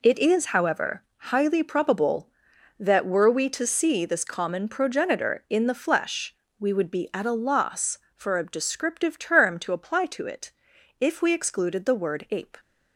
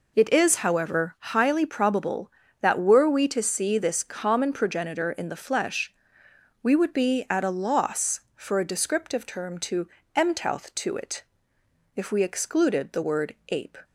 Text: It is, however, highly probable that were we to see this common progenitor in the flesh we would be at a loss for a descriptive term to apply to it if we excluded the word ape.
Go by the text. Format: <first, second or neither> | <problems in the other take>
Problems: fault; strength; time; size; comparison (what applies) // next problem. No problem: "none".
first | pauses between "flesh" and "we"; noticeable; at 5.9 s; 0.68 s long; slight in the first // says "mtouth" for "apply"; at 10.1 s // pauses between "it" and "if"; noticeable; at 11.2 s; 0.72 s long; noticeable in the first